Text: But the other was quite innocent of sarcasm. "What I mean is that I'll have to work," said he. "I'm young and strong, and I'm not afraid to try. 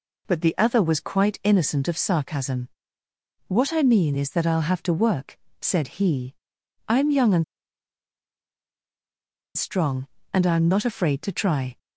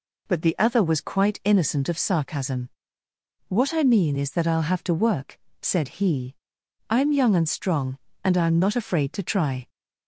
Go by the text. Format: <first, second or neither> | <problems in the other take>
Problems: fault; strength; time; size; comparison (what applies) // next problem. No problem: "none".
second | pauses between "and" and "strong"; strong; at 7.4 s; 2.1 s long